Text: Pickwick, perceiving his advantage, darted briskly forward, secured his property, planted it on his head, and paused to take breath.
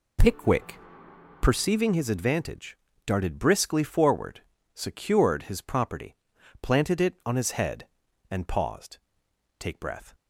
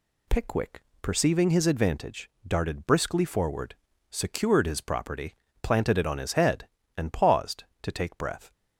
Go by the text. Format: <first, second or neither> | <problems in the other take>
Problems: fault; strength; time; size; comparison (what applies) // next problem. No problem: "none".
second | skips "to"; at 9.2 s